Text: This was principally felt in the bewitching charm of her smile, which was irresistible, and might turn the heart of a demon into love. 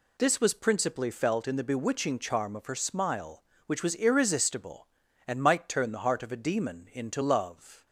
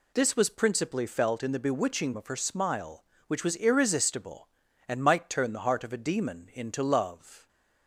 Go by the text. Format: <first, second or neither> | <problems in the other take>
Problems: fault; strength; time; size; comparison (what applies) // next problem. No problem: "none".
first | skips "charm"; at 2.1 s